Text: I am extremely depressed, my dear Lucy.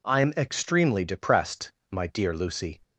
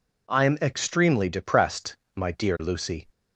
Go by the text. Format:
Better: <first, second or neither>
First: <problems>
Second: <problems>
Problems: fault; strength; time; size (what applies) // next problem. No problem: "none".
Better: neither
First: none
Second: none